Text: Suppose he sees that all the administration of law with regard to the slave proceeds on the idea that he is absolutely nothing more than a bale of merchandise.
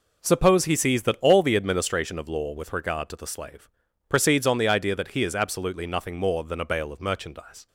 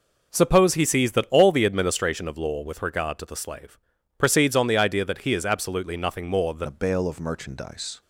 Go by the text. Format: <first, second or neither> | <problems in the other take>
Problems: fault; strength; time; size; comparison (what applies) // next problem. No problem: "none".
first | pauses between "slave" and "proceeds"; at 3.7 s; 0.42 s long; also in the first // changes voice at "a"; from 6.6 s on; 1.4 s long